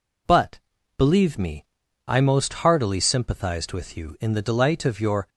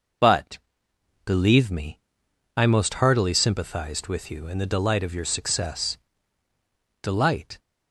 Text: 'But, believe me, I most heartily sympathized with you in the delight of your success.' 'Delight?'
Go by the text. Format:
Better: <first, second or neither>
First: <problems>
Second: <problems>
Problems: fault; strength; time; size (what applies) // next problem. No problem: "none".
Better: second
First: stops before "success Delight"; at 5.2 s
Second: none